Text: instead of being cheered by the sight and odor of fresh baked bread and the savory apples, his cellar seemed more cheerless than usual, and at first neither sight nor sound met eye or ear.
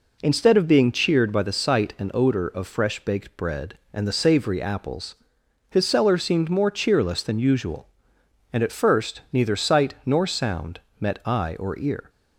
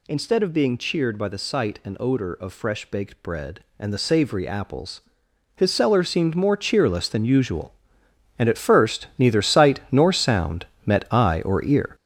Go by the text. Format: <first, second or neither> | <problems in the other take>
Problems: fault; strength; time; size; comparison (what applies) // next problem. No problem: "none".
first | gets louder; strong; throughout; 8.5 dB // pauses between "sound" and "met"; slight; at 10.6 s; 0.20 s long; slight in the first